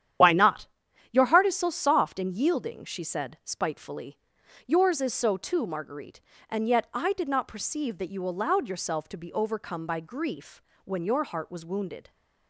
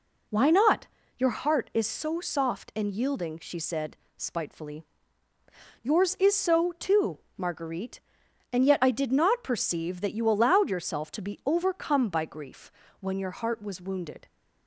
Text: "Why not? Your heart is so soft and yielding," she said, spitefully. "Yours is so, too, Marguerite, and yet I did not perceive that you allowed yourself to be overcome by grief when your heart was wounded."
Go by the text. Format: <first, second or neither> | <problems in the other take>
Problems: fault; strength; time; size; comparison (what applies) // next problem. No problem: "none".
second | loses the start of "Why"; at 0.2 s; 65 ms // starts louder than the rest; strong; until 1.6 s; 10 dB // pauses between "grief" and "when"; slight; at 10.6 s; 0.22 s long; slight in the second